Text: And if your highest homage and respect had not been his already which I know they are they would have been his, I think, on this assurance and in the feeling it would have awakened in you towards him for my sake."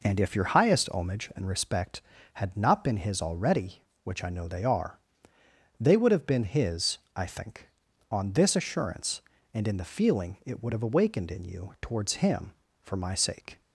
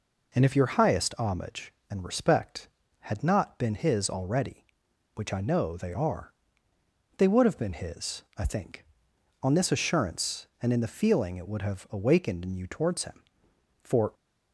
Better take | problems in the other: first | pauses between "are" and "they"; noticeable; at 6.3 s; 0.86 s long; noticeable in the first // stops before "my sake"; at 14.1 s

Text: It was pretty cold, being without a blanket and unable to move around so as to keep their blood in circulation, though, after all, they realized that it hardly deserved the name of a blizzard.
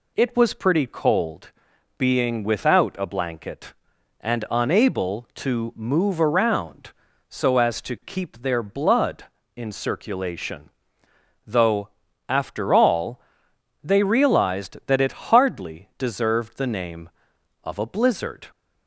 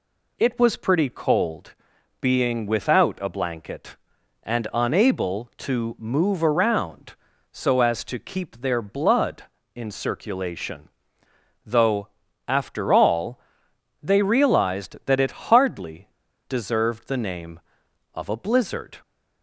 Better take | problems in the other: first | pauses between "hardly" and "deserved"; at 16.0 s; 0.41 s long

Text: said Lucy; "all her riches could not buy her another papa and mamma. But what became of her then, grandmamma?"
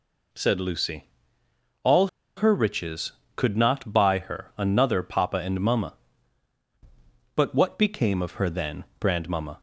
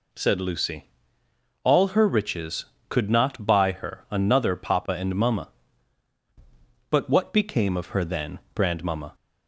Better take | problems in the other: second | pauses between "all" and "her"; slight; at 2.0 s; 0.29 s long

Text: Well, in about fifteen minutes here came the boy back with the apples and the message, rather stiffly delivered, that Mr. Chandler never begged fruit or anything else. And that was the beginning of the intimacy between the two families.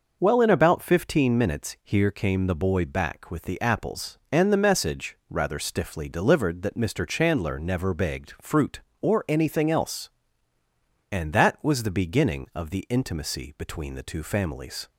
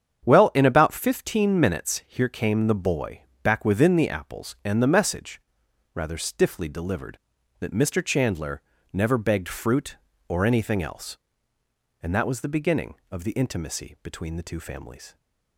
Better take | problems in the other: first | starts louder than the rest; strong; until 1.3 s; 8.5 dB // pauses between "boy" and "back"; slight; at 3.2 s; 0.18 s long // says "within" for "with"; at 3.6 s // pauses between "Chandler" and "never"; slight; at 8.6 s; 0.32 s long

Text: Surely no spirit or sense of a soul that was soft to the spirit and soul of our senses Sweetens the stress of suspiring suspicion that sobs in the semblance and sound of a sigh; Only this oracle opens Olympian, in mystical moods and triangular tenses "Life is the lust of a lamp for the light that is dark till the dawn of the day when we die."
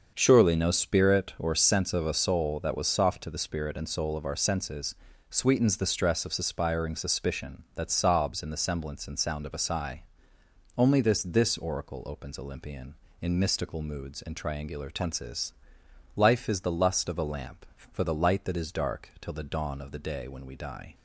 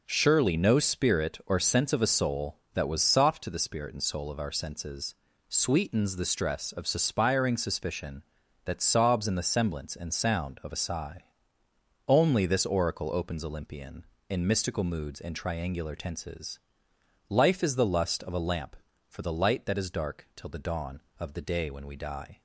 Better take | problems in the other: second | starts louder than the rest; until 1.1 s; 6.5 dB // pauses between "senses" and "Sweetens"; slight; at 4.9 s; 0.36 s long; slight in the second // says "this" twice; at 11.2 s // pauses between "tenses" and "Life"; noticeable; at 15.5 s; 0.62 s long; noticeable in the second

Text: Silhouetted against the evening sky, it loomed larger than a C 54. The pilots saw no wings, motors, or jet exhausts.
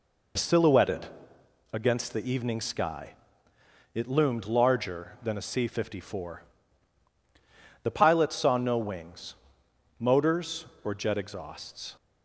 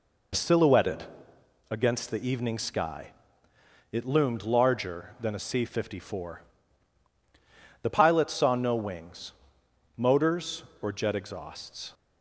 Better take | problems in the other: neither | pauses between "Silhouetted" and "against"; noticeable; the same in both

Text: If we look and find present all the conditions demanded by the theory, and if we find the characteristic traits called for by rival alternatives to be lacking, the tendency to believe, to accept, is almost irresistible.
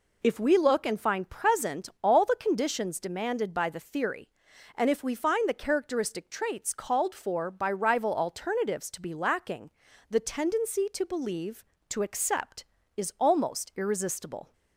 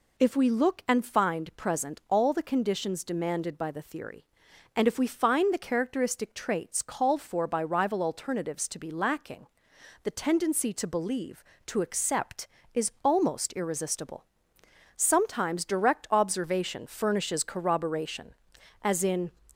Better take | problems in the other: first | goes on to say "Sometimes direct observation furnishes corroboration as in"; strong; from 14.9 s on; 4.3 s long

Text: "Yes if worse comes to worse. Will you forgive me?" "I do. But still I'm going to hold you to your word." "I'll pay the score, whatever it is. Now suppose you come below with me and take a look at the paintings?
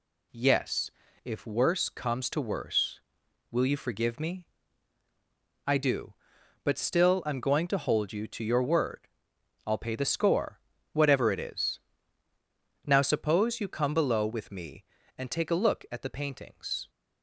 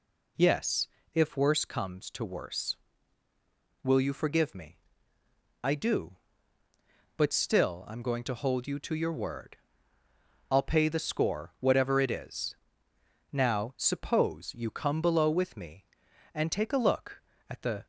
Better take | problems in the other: first | pauses between "Yes" and "if"; slight; at 0.8 s; 0.24 s long; slight in the first // stops before "paintings"; at 17.8 s

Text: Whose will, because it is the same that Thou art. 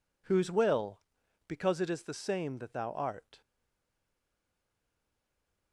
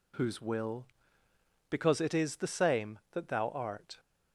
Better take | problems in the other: second | stays silent after the last word; from 3.4 s on; 2.3 s long

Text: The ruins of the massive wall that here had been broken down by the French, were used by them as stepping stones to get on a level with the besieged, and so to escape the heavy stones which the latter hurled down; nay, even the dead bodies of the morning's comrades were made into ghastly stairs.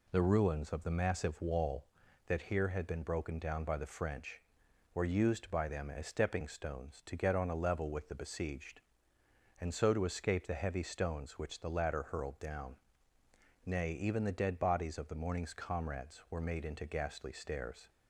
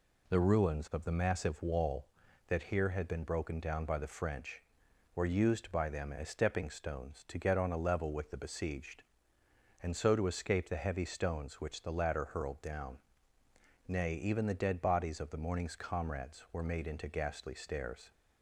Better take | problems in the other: neither | none

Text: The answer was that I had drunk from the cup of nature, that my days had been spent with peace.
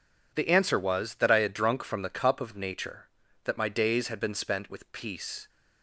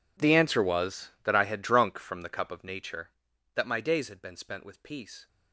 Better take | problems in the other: first | gets quieter; strong; throughout; 22.5 dB

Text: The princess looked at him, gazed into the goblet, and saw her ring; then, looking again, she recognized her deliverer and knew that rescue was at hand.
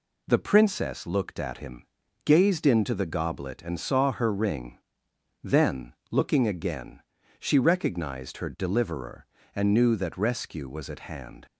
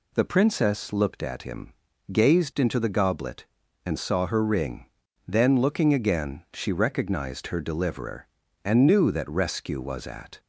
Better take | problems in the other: first | stops before "hand"; at 10.3 s

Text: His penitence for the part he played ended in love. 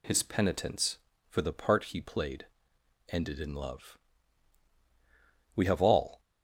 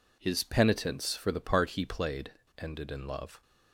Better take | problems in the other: second | pauses between "played" and "ended"; noticeable; at 2.4 s; 0.64 s long; slight in the second // goes on to say "We have all"; noticeable; from 5.5 s on; 0.64 s long

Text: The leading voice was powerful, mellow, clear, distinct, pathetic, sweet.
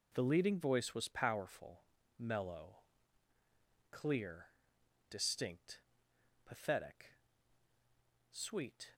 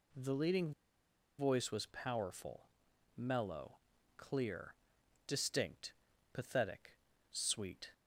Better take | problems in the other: first | pauses between "leading" and "voice"; noticeable; at 0.7 s; 0.66 s long

